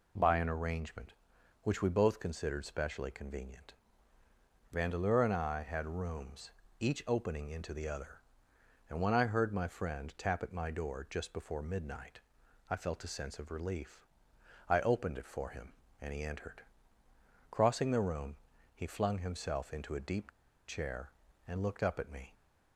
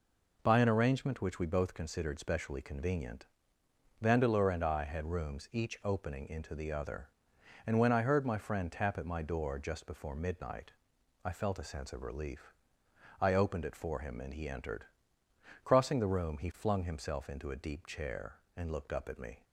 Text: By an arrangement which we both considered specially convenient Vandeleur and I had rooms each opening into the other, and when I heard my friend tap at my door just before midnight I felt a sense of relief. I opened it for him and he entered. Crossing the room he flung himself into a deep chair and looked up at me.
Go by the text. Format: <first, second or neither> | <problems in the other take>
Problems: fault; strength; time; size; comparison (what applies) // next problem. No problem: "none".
second | pauses between "convenient" and "Vandeleur"; noticeable; at 3.7 s; 0.98 s long; noticeable in the second // pauses between "rooms" and "each"; slight; at 6.5 s; 0.28 s long // pauses between "midnight" and "I"; noticeable; at 12.2 s; 0.50 s long; noticeable in the second // pauses between "room" and "he"; at 18.3 s; 0.38 s long // pauses between "deep" and "chair"; at 20.3 s; 0.37 s long